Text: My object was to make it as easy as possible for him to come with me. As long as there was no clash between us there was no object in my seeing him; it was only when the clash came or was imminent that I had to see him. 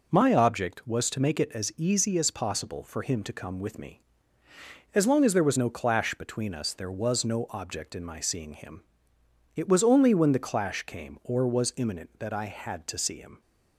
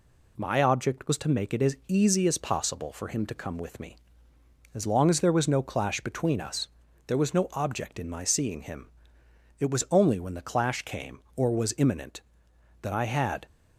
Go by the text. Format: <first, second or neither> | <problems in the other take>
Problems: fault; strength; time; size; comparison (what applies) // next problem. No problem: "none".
first | pauses between "us" and "there"; at 6.6 s; 0.40 s long // stops before "to see him"; at 13.4 s